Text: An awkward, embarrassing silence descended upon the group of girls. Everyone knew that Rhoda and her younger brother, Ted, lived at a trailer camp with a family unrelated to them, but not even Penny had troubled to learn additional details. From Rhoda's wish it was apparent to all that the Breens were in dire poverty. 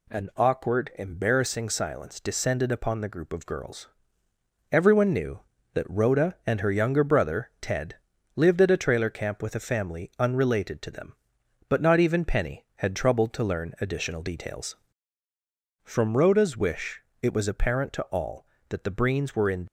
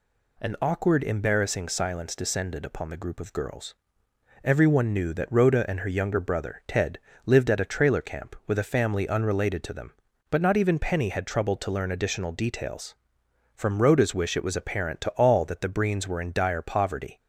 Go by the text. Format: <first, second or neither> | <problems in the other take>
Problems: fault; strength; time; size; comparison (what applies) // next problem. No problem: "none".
second | pauses between "wish" and "it"; slight; at 17.0 s; 0.18 s long // stops before "dire poverty"; at 19.6 s